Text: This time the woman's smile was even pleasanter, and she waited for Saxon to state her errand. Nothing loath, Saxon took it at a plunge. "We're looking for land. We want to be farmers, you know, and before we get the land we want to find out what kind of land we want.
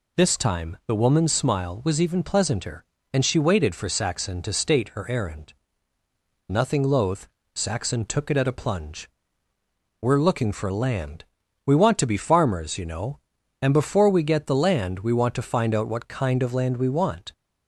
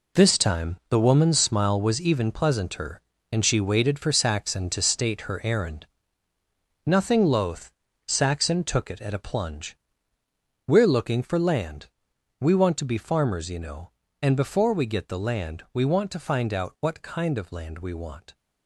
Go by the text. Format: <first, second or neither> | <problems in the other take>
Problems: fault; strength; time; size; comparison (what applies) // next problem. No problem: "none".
first | gets quieter; strong; throughout; 10 dB